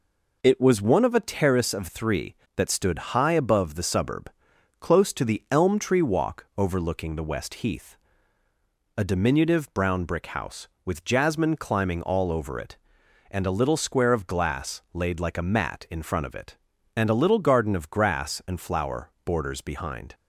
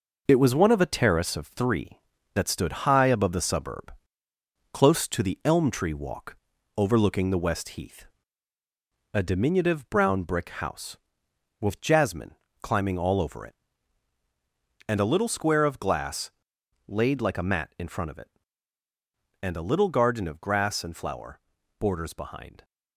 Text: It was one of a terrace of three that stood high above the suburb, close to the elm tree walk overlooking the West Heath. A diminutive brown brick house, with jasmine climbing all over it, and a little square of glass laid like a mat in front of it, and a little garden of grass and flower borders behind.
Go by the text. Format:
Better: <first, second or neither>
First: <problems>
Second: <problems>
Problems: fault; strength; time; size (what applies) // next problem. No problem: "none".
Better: first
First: none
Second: gets quieter; noticeable; throughout; 5.5 dB // pauses between "walk" and "overlooking"; at 6.3 s; 0.40 s long // pauses between "jasmine" and "climbing"; slight; at 12.3 s; 0.30 s long // pauses between "glass" and "laid"; noticeable; at 16.3 s; 0.56 s long // pauses between "flower" and "borders"; at 21.3 s; 0.40 s long